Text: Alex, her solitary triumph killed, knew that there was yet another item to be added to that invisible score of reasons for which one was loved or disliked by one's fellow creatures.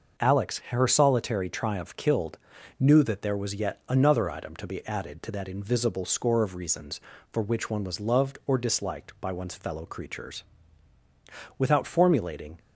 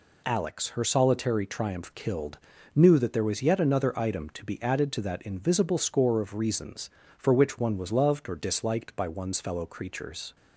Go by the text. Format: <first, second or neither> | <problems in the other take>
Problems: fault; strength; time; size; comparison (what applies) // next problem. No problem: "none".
second | starts louder than the rest; noticeable; until 1.2 s; 6 dB // goes on to say "Without formulating"; noticeable; from 11.5 s on; 1.0 s long